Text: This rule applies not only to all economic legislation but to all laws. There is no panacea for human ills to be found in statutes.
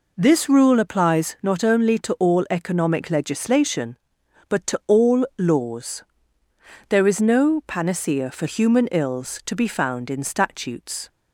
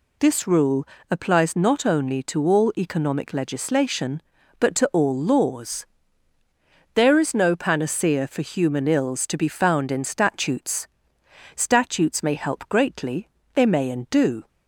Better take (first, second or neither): first